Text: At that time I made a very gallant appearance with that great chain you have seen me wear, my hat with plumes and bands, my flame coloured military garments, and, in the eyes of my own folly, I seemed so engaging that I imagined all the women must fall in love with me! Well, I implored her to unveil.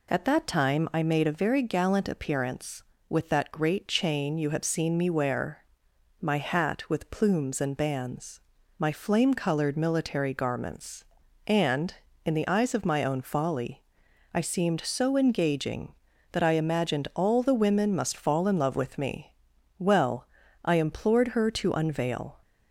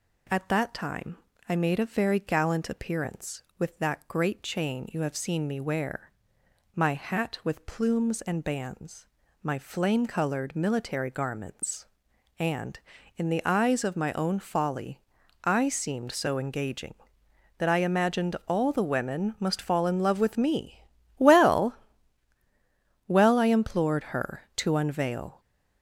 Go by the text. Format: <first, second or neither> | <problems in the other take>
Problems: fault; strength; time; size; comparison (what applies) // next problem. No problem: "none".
first | pauses between "time" and "I"; slight; at 1.1 s; 0.30 s long // says "Well" twice; at 23.0 s